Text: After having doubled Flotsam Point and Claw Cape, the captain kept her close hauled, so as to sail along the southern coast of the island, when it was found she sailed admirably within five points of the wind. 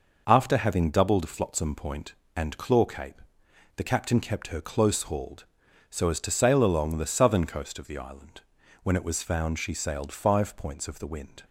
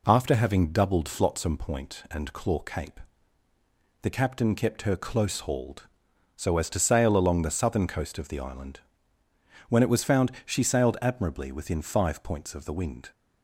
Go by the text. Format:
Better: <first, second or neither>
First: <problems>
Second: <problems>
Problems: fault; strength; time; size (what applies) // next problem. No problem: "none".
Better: second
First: skips "admirably within"; at 10.1 s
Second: none